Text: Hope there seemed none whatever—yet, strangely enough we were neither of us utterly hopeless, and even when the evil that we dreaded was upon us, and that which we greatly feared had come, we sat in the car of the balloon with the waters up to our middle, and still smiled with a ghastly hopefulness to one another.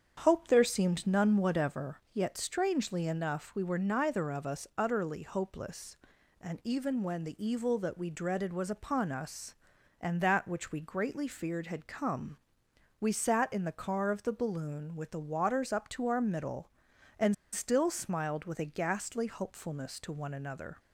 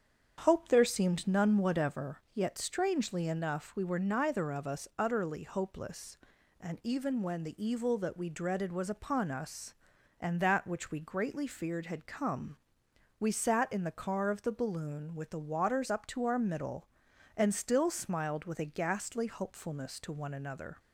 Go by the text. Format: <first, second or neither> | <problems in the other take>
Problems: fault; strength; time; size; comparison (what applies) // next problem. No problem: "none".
second | starts louder than the rest; strong; until 1.2 s; 8 dB; strong in the second // pauses between "and" and "still"; slight; at 17.3 s; 0.19 s long